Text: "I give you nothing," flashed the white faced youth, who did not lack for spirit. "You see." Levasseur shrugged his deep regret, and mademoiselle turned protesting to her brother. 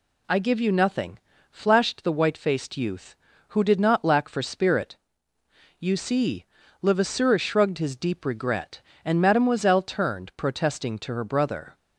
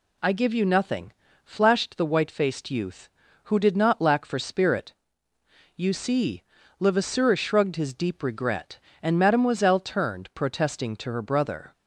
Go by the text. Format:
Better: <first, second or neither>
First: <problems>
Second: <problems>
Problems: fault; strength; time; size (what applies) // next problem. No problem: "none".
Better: neither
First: none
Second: none